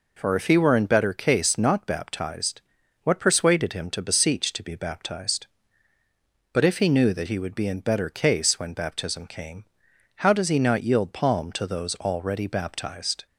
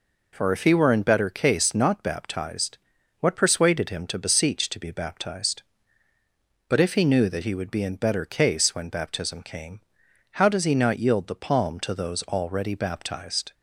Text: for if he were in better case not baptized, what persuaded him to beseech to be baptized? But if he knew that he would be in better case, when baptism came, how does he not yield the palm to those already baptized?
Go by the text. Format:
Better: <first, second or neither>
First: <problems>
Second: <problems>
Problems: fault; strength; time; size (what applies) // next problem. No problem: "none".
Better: second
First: skips "the"; at 11.1 s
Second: none